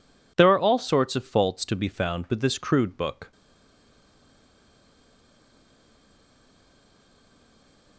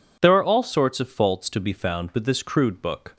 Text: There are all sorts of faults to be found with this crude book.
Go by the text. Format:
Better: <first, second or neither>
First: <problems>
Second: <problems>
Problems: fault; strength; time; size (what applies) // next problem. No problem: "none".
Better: second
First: stays silent after the last word; strong; from 3.3 s on; 4.6 s long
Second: none